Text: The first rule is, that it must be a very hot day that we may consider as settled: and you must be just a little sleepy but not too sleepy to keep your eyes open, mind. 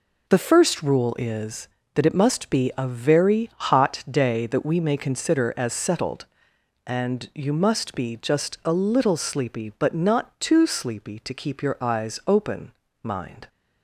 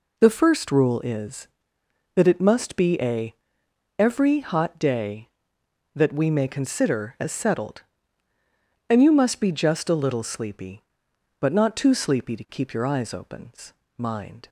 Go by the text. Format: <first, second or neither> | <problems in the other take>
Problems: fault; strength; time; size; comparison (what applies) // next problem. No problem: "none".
first | says "every" for "very"; at 3.9 s